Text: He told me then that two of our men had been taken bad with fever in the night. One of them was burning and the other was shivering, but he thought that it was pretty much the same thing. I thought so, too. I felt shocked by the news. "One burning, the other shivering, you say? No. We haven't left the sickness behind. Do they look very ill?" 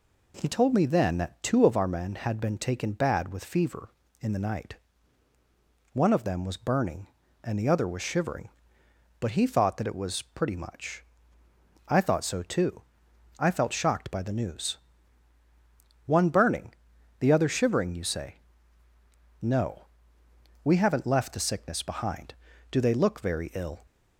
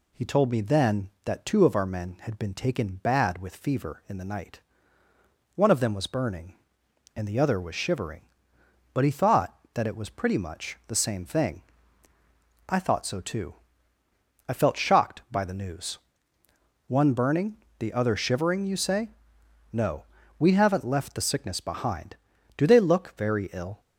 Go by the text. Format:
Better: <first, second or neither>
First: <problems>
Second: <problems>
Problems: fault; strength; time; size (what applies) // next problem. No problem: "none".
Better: second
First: skips "the same thing"; at 11.4 s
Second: none